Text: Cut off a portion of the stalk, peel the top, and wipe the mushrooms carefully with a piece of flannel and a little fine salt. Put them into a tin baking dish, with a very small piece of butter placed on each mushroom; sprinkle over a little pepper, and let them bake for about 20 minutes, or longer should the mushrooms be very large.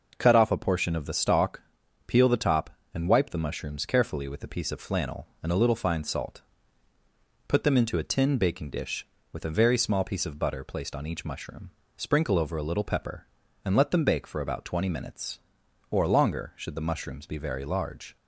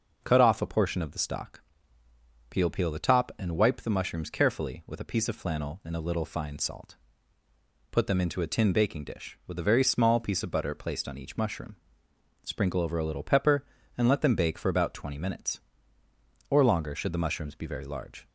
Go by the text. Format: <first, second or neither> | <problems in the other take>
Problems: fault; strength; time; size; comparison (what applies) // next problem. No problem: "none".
first | says "peel" twice; at 2.6 s